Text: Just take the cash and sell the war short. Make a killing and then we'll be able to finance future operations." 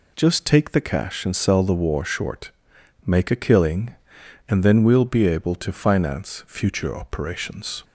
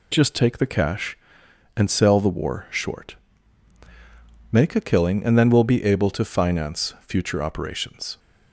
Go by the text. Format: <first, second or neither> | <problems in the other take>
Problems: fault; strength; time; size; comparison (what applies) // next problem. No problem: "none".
neither | none